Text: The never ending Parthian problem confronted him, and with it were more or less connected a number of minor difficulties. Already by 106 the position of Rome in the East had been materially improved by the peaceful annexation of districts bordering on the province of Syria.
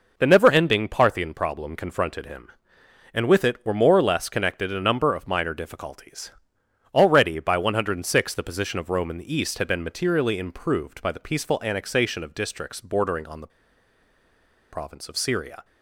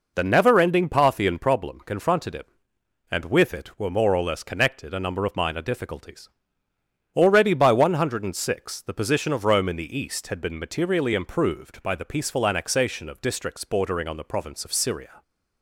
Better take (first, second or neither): second